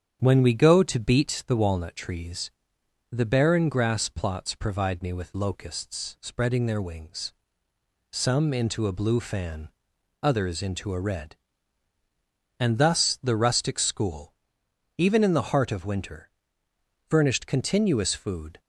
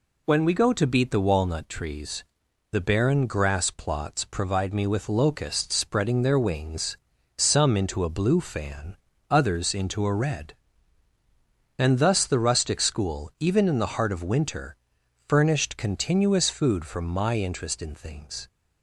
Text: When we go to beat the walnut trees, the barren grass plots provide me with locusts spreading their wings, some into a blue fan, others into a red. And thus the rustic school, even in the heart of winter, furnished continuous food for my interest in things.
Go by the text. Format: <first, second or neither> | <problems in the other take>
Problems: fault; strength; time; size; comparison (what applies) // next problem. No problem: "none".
second | starts louder than the rest; strong; until 1.2 s; 8.5 dB // stops before "for my interest in things"; at 18.6 s